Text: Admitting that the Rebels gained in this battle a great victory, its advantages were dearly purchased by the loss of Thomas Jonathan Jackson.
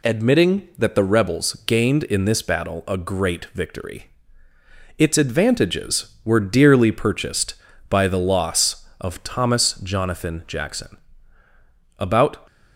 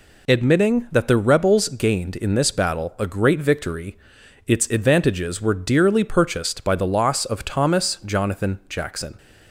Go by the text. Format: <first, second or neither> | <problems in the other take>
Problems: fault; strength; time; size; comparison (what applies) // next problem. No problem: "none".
second | goes on to say "About"; slight; from 11.9 s on; 0.48 s long